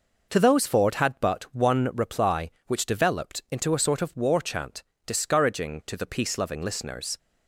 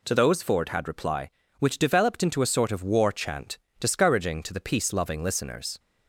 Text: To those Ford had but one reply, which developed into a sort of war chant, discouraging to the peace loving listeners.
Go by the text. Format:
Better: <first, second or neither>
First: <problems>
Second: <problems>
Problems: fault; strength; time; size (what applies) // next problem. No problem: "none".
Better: first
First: none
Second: skips "but one"; at 0.8 s